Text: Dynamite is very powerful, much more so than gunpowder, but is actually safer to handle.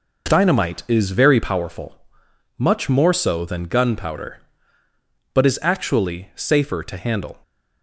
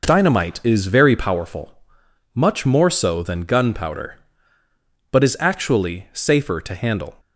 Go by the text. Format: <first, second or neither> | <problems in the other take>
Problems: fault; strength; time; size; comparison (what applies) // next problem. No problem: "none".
neither | none